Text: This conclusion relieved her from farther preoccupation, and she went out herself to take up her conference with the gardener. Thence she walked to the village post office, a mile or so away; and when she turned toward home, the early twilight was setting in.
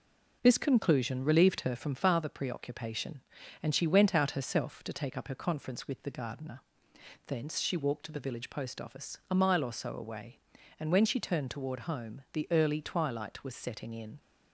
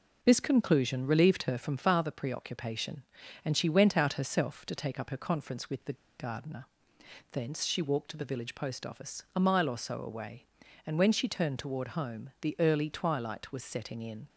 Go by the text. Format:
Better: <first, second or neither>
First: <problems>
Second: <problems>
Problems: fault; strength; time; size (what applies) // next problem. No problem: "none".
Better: first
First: none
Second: pauses between "the" and "gardener"; slight; at 5.9 s; 0.25 s long